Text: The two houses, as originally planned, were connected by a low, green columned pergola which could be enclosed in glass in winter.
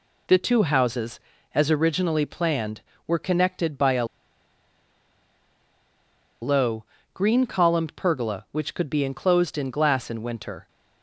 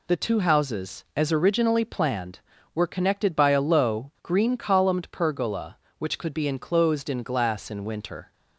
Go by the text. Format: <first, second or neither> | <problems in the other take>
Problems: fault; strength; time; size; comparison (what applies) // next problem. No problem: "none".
second | pauses between "a" and "low"; strong; at 4.0 s; 2.3 s long